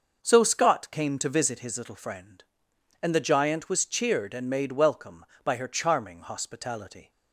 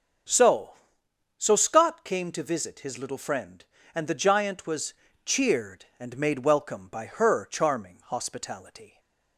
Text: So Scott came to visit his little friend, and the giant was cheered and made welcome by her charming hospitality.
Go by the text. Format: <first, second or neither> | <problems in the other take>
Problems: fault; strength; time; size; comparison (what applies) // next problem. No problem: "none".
first | starts louder than the rest; until 1.9 s; 7 dB; also in the first // says "So" twice; at 1.3 s // pauses between "was" and "cheered"; slight; at 4.9 s; 0.30 s long // stays silent after the last word; slight; from 8.8 s on; 0.5 s long